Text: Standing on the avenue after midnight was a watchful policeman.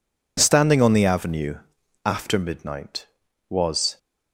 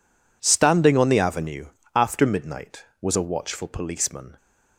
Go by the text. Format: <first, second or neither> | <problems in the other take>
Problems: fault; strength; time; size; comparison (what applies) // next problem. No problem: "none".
second | pauses between "avenue" and "after"; noticeable; at 1.5 s; 0.48 s long; slight in the second // stops before "a watchful policeman"; at 3.9 s